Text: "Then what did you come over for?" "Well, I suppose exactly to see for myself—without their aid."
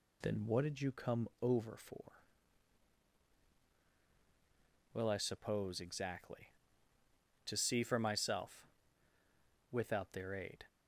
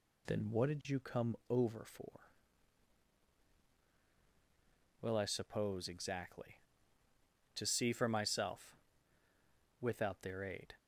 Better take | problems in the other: neither | none

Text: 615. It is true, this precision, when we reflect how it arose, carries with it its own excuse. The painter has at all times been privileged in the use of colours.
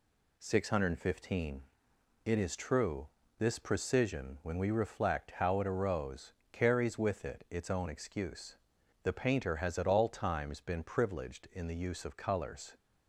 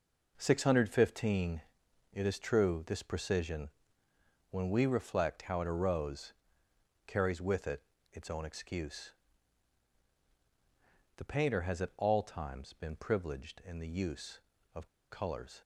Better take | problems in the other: first | pauses between "it" and "its"; slight; at 7.8 s; 0.30 s long // pauses between "of" and "colours"; slight; at 14.8 s; 0.23 s long

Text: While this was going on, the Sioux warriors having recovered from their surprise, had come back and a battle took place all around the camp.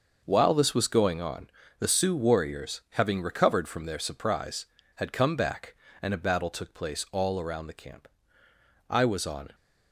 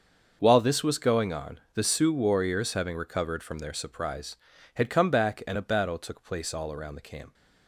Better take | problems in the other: second | starts louder than the rest; noticeable; until 1.2 s; 6 dB; also in the second // goes on to say "I was on"; noticeable; from 8.8 s on; 0.66 s long

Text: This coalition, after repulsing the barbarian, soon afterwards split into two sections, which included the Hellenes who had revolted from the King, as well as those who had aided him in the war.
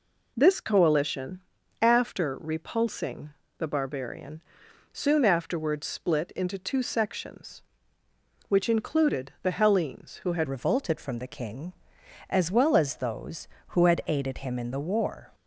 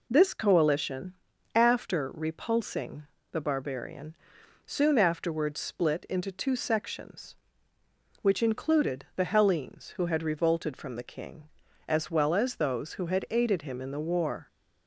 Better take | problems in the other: second | pauses between "repulsing" and "the"; slight; at 3.3 s; 0.28 s long; slight in the second // changes voice at "revolted"; from 10.4 s on; 4.9 s long

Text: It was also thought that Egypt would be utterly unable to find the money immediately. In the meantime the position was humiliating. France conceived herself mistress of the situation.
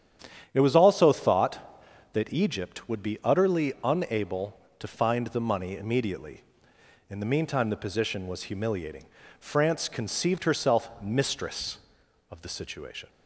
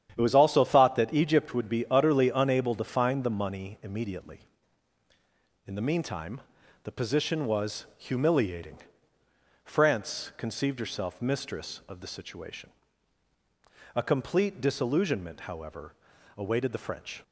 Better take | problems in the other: first | starts louder than the rest; strong; until 1.1 s; 9.5 dB; strong in the first // pauses between "meantime" and "the"; at 6.4 s; 0.42 s long // goes on to say "A complete disillusionment however awaited the French"; strong; from 13.9 s on; 3.2 s long

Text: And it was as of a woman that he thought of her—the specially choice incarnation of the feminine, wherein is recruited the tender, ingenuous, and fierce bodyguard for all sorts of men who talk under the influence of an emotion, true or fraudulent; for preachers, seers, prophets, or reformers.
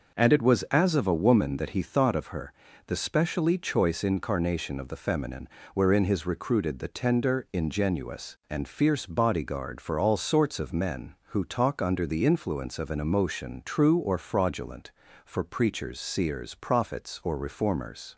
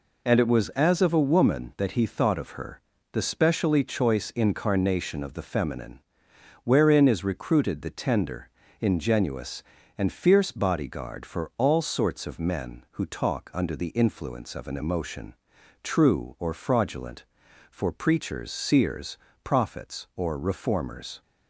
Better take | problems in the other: second | says "his" for "is"; at 6.0 s

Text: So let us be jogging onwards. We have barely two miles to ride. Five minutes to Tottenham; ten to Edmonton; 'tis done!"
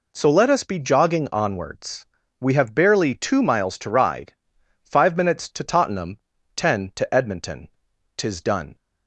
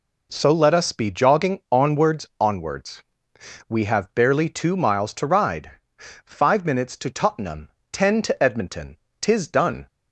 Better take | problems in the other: first | says "onwards" twice; at 2.3 s

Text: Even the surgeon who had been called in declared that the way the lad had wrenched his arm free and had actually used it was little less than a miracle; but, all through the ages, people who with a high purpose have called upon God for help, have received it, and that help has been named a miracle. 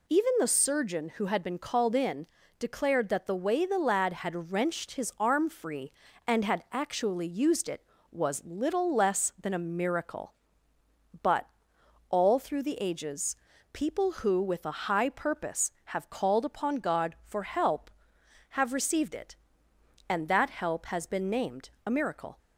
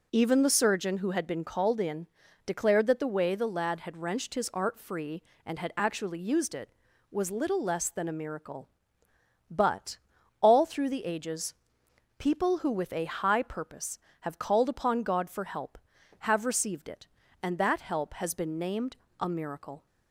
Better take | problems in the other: first | pauses between "in" and "declared"; at 2.0 s; 0.38 s long; slight in the first // says "art" for "arm"; at 4.5 s // pauses between "named" and "a"; slight; at 18.9 s; 0.22 s long

